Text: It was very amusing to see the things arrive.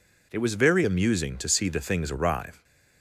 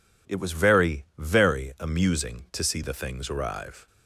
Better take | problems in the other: first | says "very" twice; at 1.1 s

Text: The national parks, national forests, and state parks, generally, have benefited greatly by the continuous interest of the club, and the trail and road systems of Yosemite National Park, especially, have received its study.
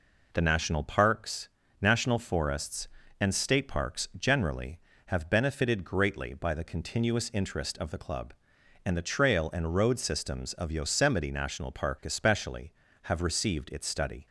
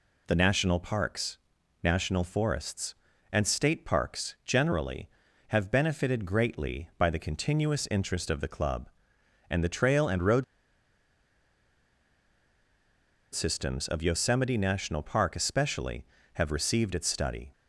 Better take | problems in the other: first | pauses between "road" and "systems"; strong; at 10.4 s; 2.9 s long

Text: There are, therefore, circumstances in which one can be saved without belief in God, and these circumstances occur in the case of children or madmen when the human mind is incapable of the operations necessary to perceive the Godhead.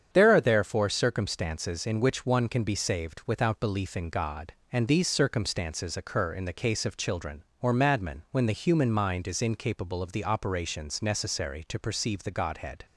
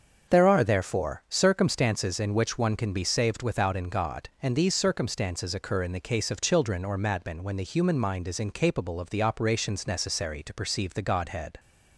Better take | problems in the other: first | starts louder than the rest; until 1.3 s; 7 dB; strong in the first // skips "belief"; at 3.7 s

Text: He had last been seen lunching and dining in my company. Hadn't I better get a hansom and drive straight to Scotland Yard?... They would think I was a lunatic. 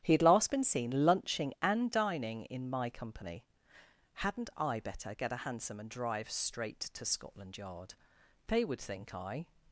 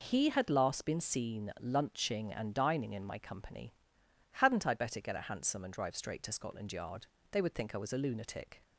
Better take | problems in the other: second | starts louder than the rest; strong; until 1.0 s; 10 dB // stops before "was a lunatic"; at 9.6 s

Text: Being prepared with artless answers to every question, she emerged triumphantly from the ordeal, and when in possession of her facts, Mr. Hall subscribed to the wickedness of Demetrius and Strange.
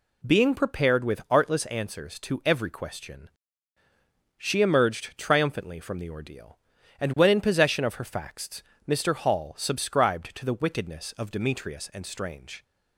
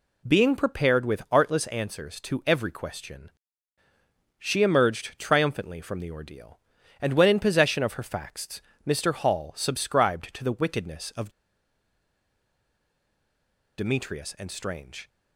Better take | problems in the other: first | pauses between "of" and "Demetrius"; strong; at 11.2 s; 2.4 s long

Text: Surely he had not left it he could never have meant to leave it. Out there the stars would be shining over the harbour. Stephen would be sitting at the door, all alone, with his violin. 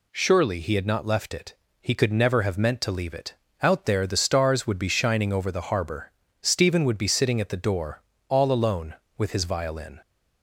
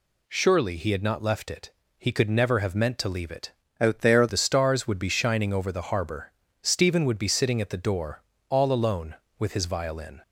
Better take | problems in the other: first | pauses between "it" and "he"; slight; at 1.6 s; 0.28 s long; slight in the first // changes voice from "Out" to "there"; from 3.7 to 4.2 s; 0.5 s long

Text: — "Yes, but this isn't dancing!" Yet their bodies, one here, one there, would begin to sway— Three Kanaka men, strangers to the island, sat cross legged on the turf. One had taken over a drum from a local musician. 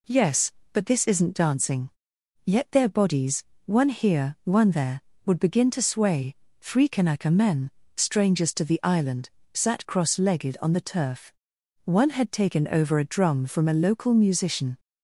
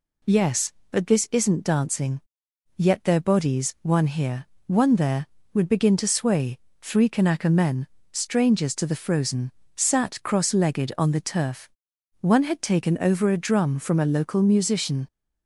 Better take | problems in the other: first | says "frozen" for "island"; at 8.9 s

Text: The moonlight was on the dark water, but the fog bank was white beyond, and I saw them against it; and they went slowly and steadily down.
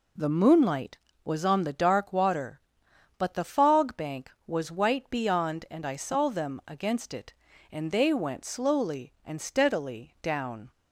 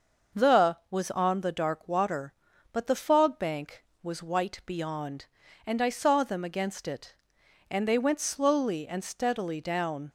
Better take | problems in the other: first | starts louder than the rest; noticeable; until 1.4 s; 6 dB // skips "moonlight"; at 0.8 s

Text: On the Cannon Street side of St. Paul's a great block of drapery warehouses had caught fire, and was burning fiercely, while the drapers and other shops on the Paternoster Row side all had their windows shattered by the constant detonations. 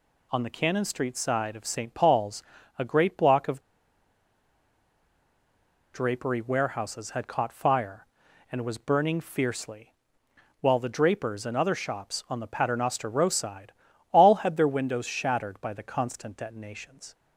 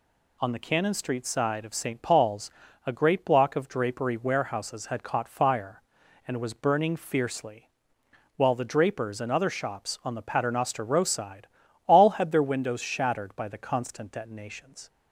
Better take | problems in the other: second | pauses between "Paul's" and "a"; slight; at 2.4 s; 0.36 s long; slight in the second // pauses between "of" and "drapery"; strong; at 3.5 s; 2.3 s long // pauses between "side" and "all"; at 13.7 s; 0.40 s long; also in the second

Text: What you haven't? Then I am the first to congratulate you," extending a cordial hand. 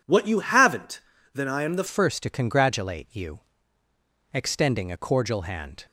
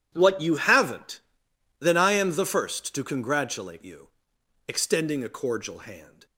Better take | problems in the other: second | changes voice at "first"; from 1.8 s on; 4.0 s long

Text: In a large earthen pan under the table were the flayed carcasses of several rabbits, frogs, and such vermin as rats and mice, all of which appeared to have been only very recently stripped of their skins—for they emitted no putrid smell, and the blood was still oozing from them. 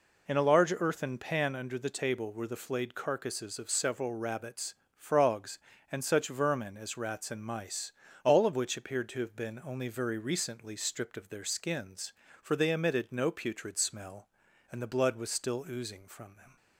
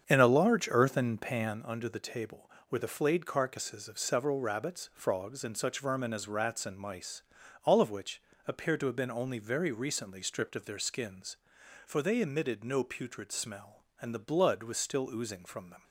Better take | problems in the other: first | starts louder than the rest; strong; until 1.6 s; 7.5 dB // pauses between "which" and "appeared"; slight; at 8.2 s; 0.26 s long

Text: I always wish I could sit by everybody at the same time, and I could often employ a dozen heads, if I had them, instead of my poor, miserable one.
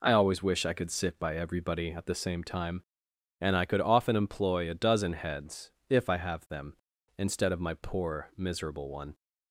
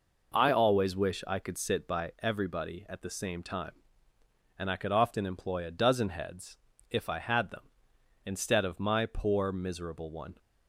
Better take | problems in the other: second | says "have" for "had"; at 6.1 s

